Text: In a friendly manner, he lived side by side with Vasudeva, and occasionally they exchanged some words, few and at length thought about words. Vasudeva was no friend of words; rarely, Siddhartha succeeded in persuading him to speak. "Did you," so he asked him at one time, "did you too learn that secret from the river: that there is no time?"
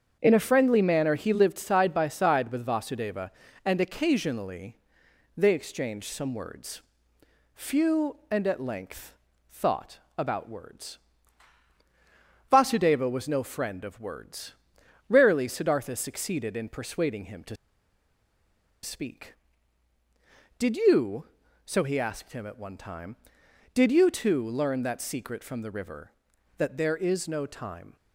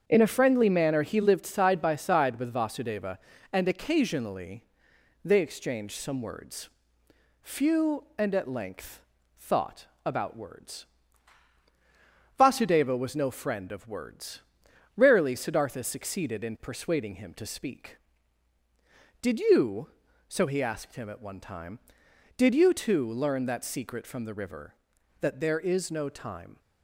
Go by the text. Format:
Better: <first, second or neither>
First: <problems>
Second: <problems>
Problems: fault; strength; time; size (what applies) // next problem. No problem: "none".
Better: second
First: starts louder than the rest; strong; until 1.2 s; 7 dB // pauses between "occasionally" and "they"; noticeable; at 4.7 s; 0.60 s long // pauses between "length" and "thought"; at 9.1 s; 0.38 s long // pauses between "thought" and "about"; slight; at 9.9 s; 0.18 s long // pauses between "to" and "speak"; strong; at 17.5 s; 1.2 s long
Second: starts louder than the rest; strong; until 1.0 s; 7 dB // pauses between "occasionally" and "they"; noticeable; at 4.6 s; 0.60 s long // pauses between "length" and "thought"; at 9.0 s; 0.38 s long // pauses between "thought" and "about"; slight; at 9.8 s; 0.18 s long